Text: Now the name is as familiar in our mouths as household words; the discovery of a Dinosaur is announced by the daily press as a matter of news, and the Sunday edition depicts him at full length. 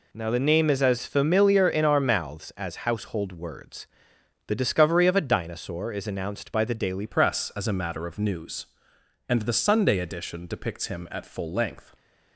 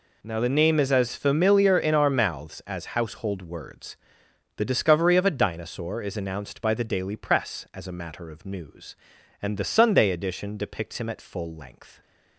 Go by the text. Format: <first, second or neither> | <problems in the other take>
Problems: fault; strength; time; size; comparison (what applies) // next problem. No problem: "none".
second | changes voice at "press"; from 7.0 s on; 4.9 s long